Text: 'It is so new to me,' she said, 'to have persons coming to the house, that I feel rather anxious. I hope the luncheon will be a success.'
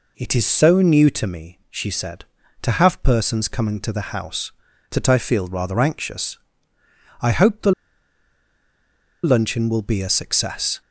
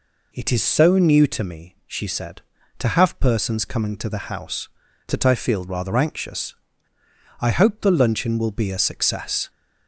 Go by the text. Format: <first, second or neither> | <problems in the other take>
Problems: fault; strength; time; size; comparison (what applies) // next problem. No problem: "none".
second | pauses between "the" and "luncheon"; strong; at 7.7 s; 1.5 s long